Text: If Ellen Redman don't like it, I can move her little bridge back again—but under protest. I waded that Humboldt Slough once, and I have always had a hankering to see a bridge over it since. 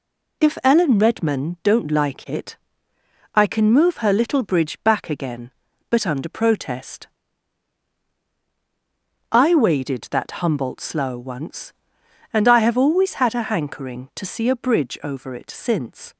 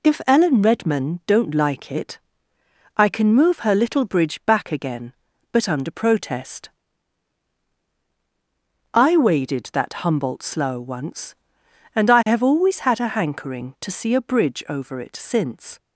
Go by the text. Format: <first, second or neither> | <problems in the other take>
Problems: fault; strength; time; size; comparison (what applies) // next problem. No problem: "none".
neither | none